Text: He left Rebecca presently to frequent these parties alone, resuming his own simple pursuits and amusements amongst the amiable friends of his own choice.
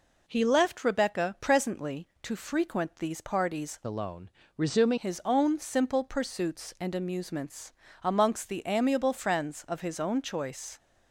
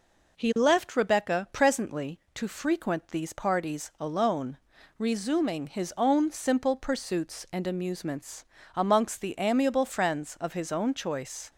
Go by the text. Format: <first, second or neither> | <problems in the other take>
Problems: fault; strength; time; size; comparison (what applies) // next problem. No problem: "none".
second | changes voice from "alone" to "resuming"; from 3.8 to 4.9 s; 1.1 s long // pauses between "amusements" and "amongst"; slight; at 7.7 s; 0.32 s long; slight in the second